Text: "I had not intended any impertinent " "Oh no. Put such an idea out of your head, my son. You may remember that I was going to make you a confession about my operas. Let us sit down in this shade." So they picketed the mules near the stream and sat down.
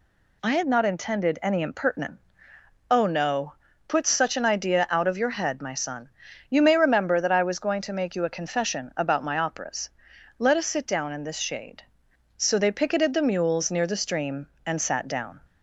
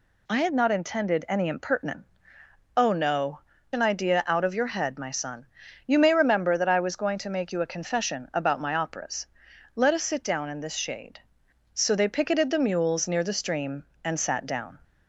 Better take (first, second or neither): first